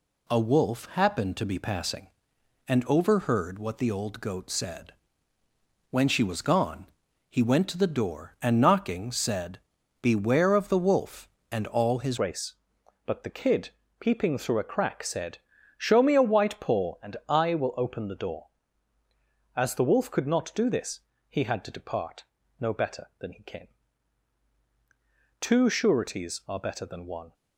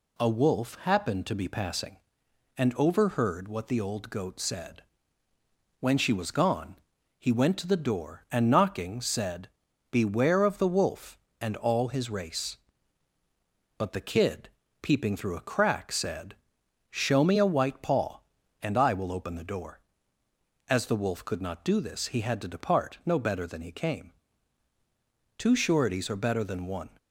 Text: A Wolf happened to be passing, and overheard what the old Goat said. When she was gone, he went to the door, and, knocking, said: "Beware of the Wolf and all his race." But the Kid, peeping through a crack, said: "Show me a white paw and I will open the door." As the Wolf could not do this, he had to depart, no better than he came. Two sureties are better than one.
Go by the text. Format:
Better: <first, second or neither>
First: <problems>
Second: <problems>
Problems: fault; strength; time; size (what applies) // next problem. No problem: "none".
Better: second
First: changes voice at "race"; from 12.1 s on; 15.2 s long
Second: none